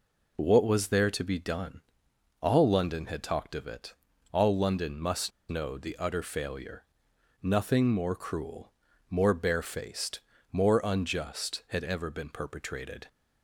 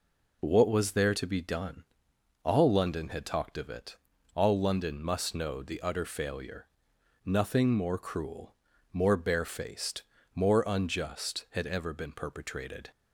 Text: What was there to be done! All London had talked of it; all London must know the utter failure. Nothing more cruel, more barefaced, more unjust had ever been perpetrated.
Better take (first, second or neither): second